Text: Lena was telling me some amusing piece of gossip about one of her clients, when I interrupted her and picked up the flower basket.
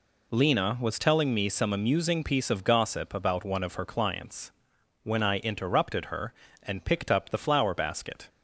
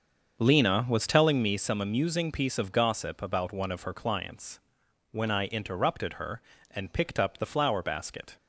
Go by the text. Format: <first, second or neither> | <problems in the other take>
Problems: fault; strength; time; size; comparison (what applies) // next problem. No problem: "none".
first | starts louder than the rest; until 1.6 s; 6.5 dB